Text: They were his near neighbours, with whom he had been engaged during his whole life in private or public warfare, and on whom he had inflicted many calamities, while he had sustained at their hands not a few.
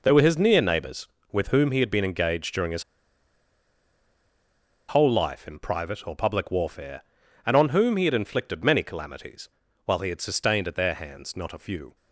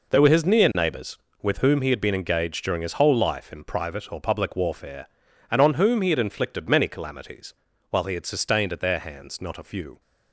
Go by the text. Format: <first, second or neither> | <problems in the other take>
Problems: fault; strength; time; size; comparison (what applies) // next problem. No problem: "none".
second | pauses between "his" and "whole"; strong; at 2.8 s; 2.0 s long